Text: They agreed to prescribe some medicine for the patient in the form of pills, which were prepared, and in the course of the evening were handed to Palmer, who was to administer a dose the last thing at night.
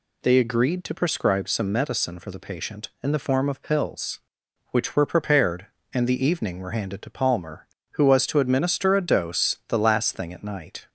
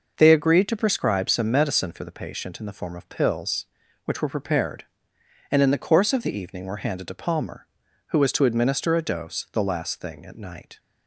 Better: second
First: skips "in the course of"; at 6.0 s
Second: none

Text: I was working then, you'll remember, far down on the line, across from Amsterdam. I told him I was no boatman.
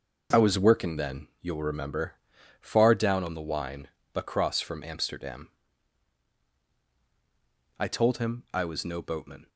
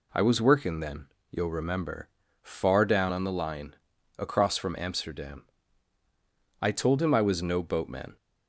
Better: second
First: says "wine" for "line"; at 3.4 s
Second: none

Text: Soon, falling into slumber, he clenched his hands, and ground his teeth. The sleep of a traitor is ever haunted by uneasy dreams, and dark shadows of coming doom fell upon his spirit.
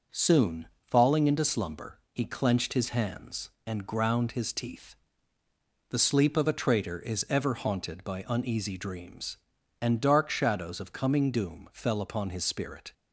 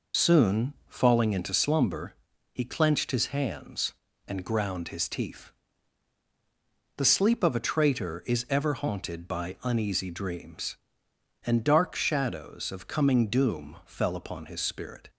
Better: first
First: none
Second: loses the start of "Soon"; at 0.1 s; 60 ms

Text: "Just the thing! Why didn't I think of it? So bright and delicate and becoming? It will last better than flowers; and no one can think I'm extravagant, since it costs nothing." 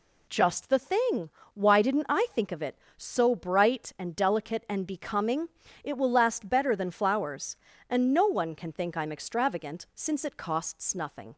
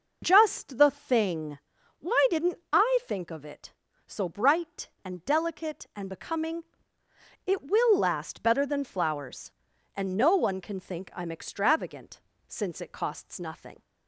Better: neither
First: none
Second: none

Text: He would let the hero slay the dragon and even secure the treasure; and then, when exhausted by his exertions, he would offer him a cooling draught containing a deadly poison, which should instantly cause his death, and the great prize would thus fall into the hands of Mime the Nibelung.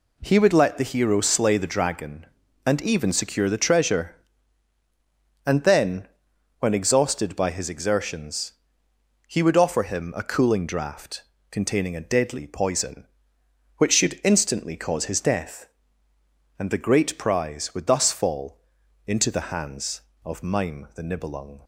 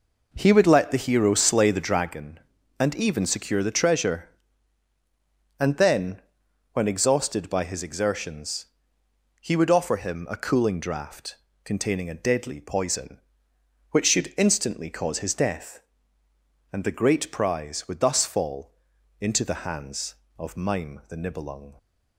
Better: first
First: pauses between "draught" and "containing"; slight; at 11.2 s; 0.28 s long // pauses between "fall" and "into"; noticeable; at 18.5 s; 0.48 s long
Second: starts louder than the rest; noticeable; until 2.1 s; 4.5 dB // pauses between "draught" and "containing"; slight; at 11.3 s; 0.28 s long // pauses between "fall" and "into"; noticeable; at 18.7 s; 0.48 s long

